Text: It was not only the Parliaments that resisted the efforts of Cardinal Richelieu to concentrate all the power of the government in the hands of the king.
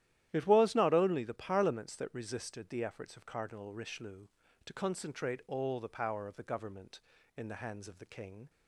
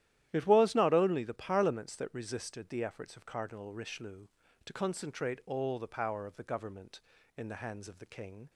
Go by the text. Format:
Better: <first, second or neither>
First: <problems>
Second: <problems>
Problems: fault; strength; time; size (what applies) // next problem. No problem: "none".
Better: neither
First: starts louder than the rest; strong; until 1.3 s; 12 dB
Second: starts louder than the rest; strong; until 1.3 s; 12 dB